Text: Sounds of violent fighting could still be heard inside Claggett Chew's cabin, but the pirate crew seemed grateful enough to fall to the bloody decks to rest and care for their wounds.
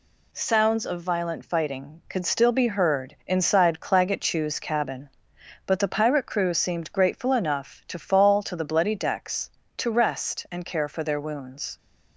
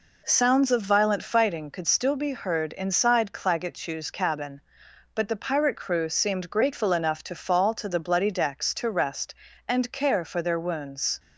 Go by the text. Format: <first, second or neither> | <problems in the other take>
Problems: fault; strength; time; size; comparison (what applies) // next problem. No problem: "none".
neither | none